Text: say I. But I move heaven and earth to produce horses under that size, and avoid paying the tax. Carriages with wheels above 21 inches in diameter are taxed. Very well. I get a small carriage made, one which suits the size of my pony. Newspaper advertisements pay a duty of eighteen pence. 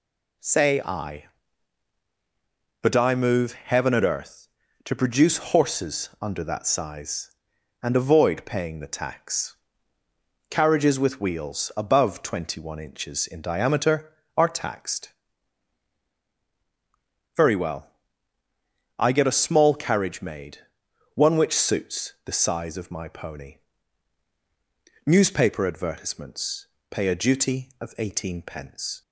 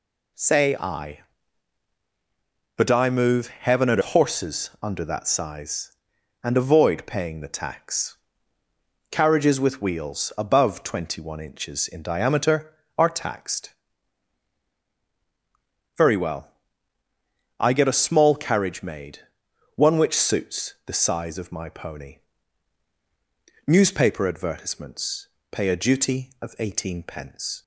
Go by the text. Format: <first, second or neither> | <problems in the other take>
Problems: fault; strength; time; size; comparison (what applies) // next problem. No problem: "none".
first | skips "earth to produce"; at 4.0 s // pauses between "advertisements" and "pay"; slight; at 25.2 s; 0.22 s long; slight in the first